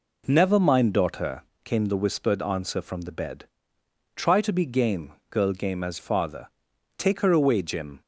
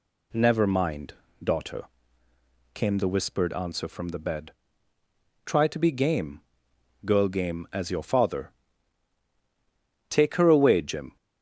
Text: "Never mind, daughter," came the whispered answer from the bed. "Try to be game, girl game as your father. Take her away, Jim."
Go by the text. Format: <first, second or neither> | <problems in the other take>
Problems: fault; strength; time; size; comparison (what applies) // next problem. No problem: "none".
second | skips "your"; at 5.9 s